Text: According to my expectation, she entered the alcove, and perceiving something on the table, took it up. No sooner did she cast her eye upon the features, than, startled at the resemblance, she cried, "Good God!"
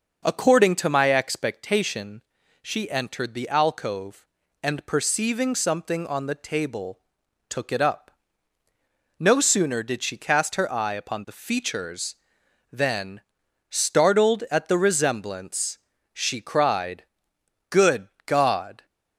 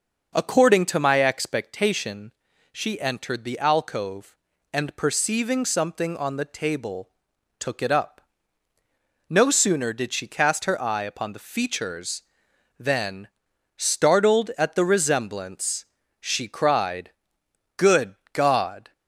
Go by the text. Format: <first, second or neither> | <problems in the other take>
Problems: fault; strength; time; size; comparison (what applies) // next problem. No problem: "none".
neither | pauses between "Good" and "God"; slight; the same in both